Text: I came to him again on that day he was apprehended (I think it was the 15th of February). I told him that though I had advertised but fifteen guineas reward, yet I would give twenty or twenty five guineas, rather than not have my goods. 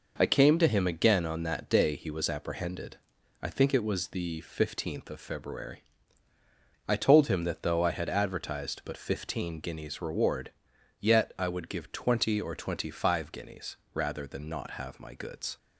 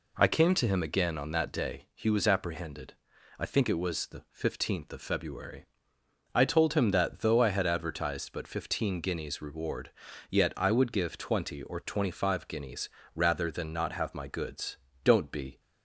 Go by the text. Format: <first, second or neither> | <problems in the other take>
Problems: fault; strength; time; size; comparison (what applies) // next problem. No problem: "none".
first | goes on to say "Don't be"; from 15.0 s on; 0.56 s long